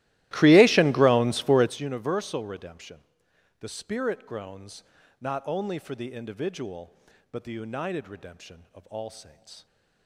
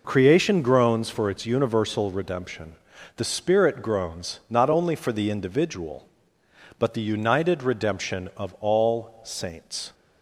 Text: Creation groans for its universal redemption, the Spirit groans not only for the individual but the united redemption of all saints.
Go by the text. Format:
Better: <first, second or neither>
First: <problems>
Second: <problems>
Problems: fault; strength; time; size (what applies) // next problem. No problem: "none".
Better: second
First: starts louder than the rest; strong; until 1.9 s; 16.5 dB // pauses between "groans" and "not"; at 4.8 s; 0.38 s long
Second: none